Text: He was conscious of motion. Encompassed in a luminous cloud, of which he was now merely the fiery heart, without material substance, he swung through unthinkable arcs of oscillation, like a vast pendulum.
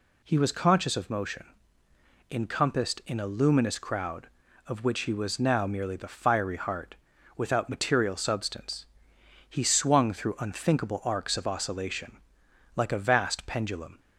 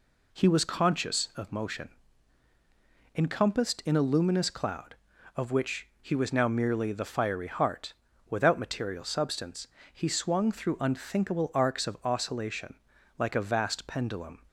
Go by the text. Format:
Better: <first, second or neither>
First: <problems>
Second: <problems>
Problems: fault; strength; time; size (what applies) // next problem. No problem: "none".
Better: second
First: says "crowd" for "cloud"; at 3.7 s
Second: none